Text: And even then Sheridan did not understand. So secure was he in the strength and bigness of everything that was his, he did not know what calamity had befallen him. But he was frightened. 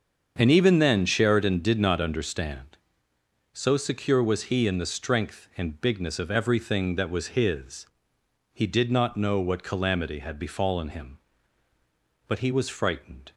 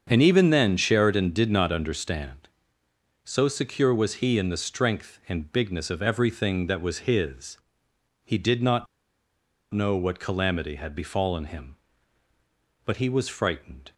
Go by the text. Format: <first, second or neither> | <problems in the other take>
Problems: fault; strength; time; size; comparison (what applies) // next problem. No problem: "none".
first | starts louder than the rest; until 1.1 s; 6.5 dB; also in the first // pauses between "not" and "know"; noticeable; at 8.8 s; 0.86 s long